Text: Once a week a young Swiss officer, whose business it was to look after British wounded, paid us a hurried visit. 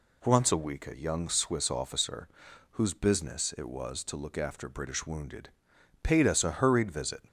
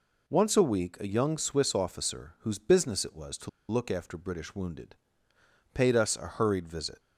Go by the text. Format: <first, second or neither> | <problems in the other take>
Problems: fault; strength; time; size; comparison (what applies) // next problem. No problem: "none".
first | pauses between "to" and "look"; slight; at 3.4 s; 0.19 s long